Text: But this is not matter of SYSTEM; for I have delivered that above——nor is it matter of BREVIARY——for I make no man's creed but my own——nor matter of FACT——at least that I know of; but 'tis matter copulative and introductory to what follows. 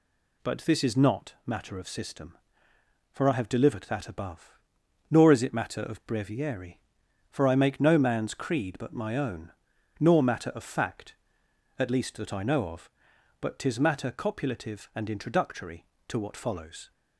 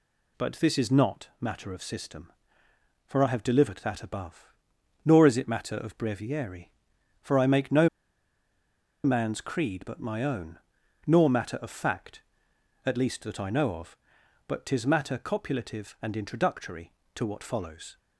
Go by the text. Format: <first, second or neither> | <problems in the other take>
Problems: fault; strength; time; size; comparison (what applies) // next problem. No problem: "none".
first | pauses between "no" and "man's"; at 7.8 s; 1.1 s long